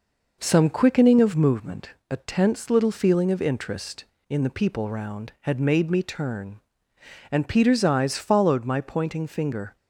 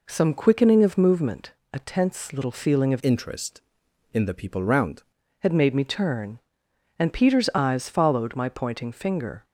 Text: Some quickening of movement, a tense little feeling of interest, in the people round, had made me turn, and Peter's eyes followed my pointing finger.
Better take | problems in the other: first | changes voice from "interest" to "round"; from 3.0 to 5.0 s; 2.0 s long

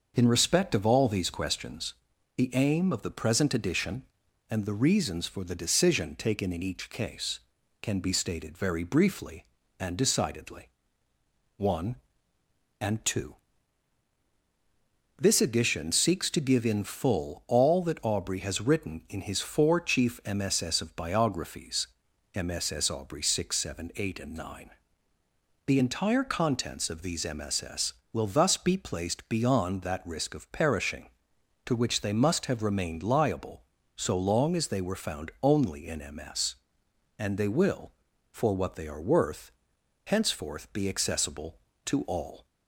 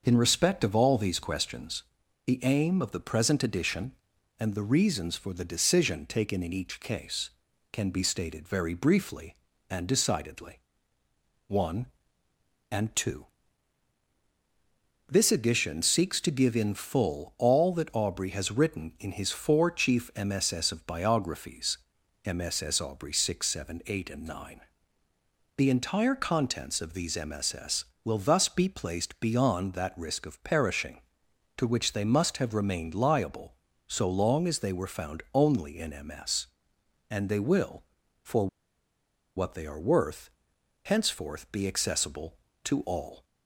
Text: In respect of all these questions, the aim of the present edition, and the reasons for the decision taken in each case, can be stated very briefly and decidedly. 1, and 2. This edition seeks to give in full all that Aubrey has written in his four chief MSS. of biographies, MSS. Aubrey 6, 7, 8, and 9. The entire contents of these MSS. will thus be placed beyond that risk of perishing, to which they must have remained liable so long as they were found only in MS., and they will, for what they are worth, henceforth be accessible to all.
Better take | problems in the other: first | starts louder than the rest; until 1.0 s; 6 dB; also in the first // pauses between "for" and "what"; noticeable; at 38.4 s; 0.90 s long

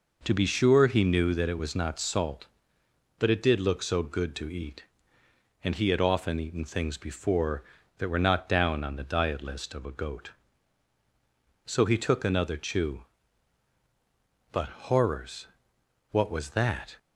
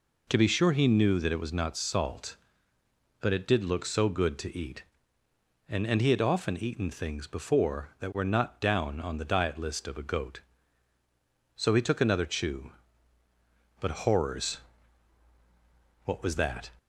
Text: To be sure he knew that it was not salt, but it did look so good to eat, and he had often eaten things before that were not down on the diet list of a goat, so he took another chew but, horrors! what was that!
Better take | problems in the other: first | says "and" twice; at 5.8 s

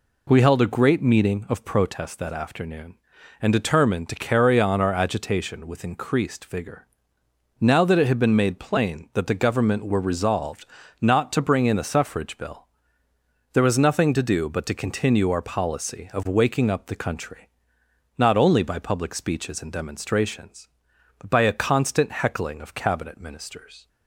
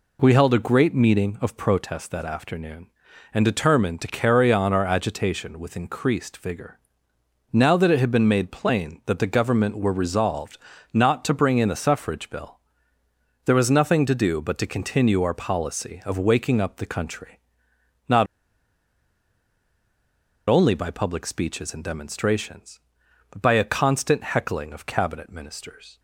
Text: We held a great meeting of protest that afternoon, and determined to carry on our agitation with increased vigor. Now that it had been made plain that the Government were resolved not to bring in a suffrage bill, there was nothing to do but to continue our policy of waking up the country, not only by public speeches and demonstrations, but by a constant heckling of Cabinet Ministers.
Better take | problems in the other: first | pauses between "resolved" and "not"; slight; at 10.5 s; 0.34 s long; slight in the first // pauses between "not" and "only"; strong; at 18.2 s; 2.2 s long

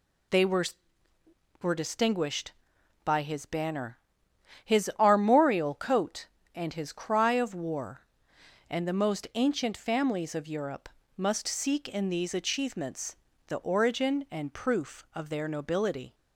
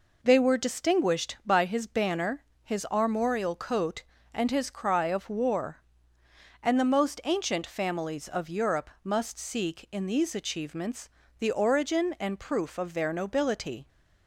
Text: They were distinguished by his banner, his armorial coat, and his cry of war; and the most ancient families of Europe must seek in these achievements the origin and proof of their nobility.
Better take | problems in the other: second | says "were" twice; at 1.6 s // pauses between "Europe" and "must"; slight; at 10.8 s; 0.28 s long // pauses between "achievements" and "the"; slight; at 13.1 s; 0.30 s long; slight in the second

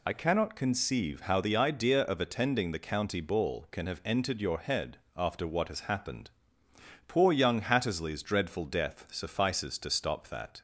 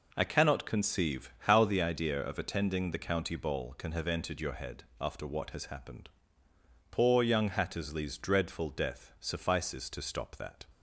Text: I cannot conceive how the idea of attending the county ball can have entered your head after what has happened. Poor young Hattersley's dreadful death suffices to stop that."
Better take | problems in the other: second | loses the start of "I"; at 0.0 s; 50 ms // pauses between "head" and "after"; slight; at 4.9 s; 0.16 s long; slight in the second

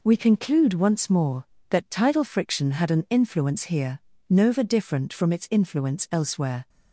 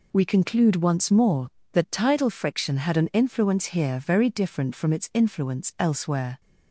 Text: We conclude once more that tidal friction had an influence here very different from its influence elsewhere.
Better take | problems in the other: second | says "nova" for "very"; at 4.2 s

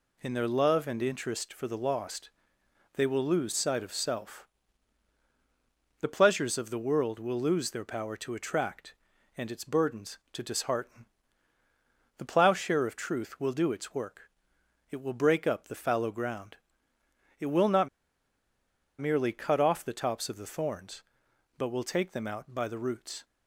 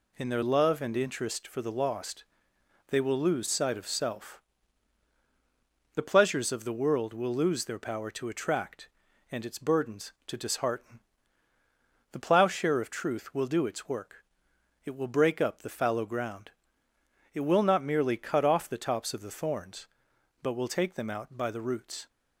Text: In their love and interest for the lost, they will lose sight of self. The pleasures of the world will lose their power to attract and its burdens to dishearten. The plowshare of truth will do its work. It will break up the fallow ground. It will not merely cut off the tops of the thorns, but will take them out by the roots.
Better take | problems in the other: second | pauses between "not" and "merely"; at 17.8 s; 1.1 s long

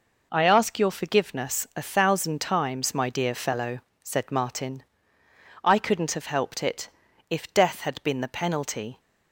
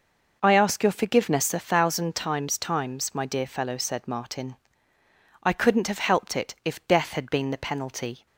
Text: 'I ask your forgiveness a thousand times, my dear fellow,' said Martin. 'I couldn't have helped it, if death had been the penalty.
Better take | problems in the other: first | says "times" twice; at 2.5 s

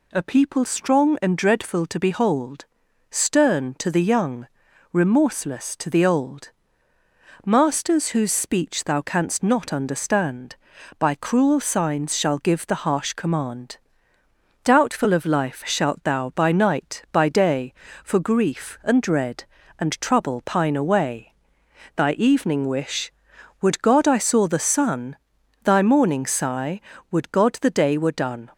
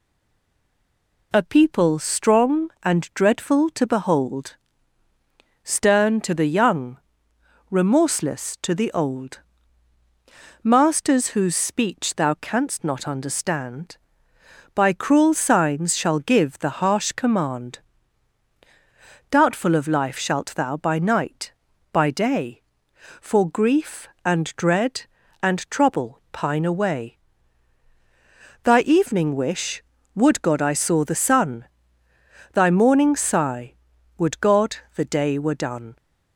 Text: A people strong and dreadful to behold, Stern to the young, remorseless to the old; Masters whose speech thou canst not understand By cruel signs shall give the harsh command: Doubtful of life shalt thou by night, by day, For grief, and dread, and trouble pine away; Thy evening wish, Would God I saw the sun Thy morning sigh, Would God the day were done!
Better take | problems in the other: first | stays silent before the first word; noticeable; until 1.3 s; 1.3 s long // pauses between "sun" and "Thy"; noticeable; at 31.6 s; 0.88 s long; noticeable in the first // pauses between "God" and "the"; slight; at 34.7 s; 0.18 s long

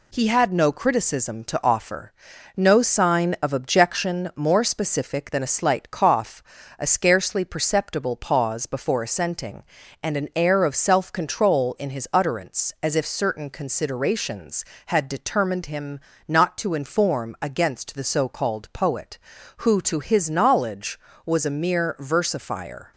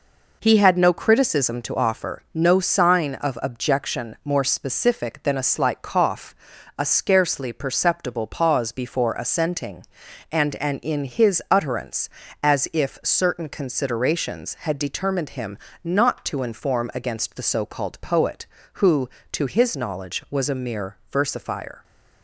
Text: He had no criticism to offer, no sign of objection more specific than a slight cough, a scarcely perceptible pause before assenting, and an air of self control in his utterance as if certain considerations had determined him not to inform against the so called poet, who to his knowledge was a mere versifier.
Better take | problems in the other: first | skips "air of self control"; at 10.7 s // pauses between "him" and "not"; slight; at 15.5 s; 0.26 s long; slight in the first // pauses between "mere" and "versifier"; slight; at 20.9 s; 0.16 s long

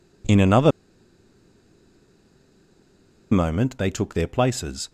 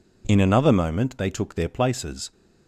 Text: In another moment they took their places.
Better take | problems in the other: second | pauses between "another" and "moment"; strong; at 0.7 s; 2.6 s long

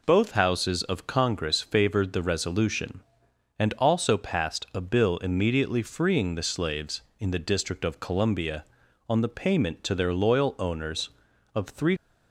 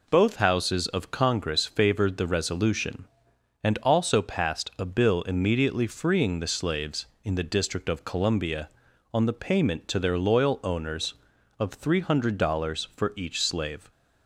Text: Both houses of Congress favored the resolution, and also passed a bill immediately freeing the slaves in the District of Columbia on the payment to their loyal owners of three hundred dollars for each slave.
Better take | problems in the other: second | stops before "hundred dollars for each slave"; at 11.9 s

